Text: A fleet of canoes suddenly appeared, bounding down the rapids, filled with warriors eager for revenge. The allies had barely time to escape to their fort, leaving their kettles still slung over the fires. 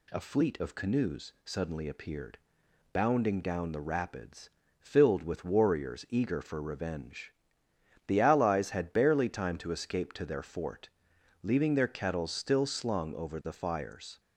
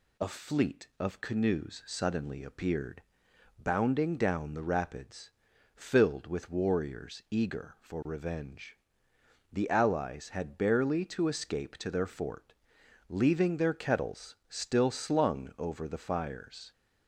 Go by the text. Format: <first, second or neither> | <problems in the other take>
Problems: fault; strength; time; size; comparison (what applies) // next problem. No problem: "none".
first | skips "time"; at 11.0 s